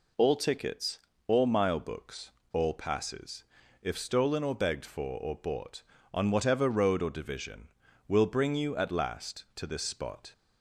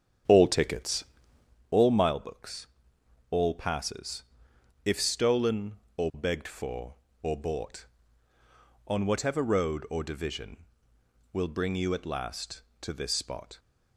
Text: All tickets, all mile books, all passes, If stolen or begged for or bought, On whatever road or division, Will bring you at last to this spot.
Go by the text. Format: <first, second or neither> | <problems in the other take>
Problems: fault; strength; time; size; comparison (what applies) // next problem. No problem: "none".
first | starts louder than the rest; strong; until 1.6 s; 8 dB